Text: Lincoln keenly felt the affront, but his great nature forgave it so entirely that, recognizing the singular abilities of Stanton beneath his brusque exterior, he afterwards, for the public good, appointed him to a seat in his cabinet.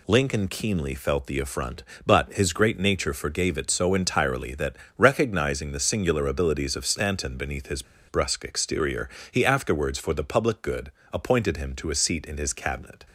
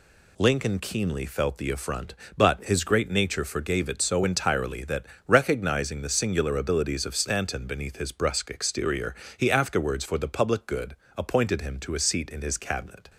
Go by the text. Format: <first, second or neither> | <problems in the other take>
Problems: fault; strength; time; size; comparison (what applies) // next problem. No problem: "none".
second | pauses between "his" and "brusque"; slight; at 7.8 s; 0.26 s long